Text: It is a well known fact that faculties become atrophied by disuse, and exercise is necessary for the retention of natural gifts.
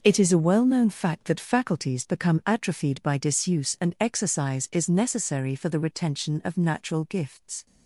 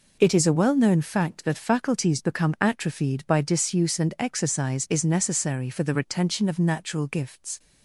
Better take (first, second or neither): second